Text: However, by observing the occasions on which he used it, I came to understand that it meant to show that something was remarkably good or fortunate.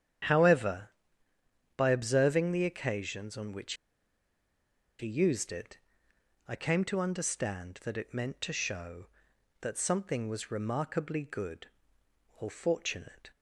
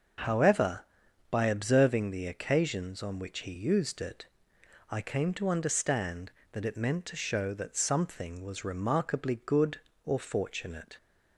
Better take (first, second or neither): second